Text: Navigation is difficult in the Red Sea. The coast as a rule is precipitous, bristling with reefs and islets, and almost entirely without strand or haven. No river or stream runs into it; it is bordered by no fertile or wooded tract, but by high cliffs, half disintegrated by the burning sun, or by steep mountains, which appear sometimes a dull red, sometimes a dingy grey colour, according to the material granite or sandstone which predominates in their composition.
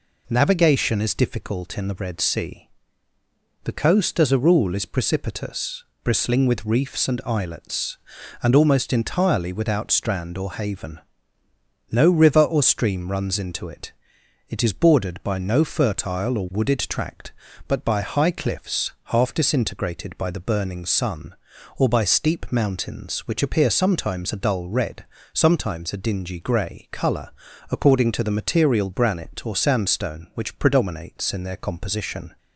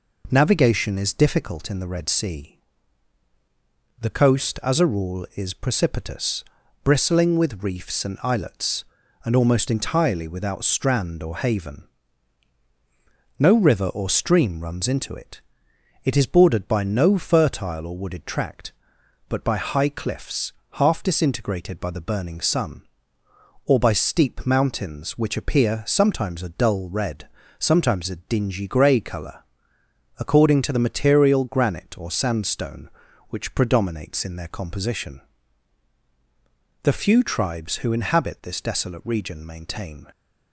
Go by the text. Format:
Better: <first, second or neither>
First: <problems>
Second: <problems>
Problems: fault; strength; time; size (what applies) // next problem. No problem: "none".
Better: first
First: none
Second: goes on to say "The few tribes who inhabit this desolate region maintain"; strong; from 36.8 s on; 3.2 s long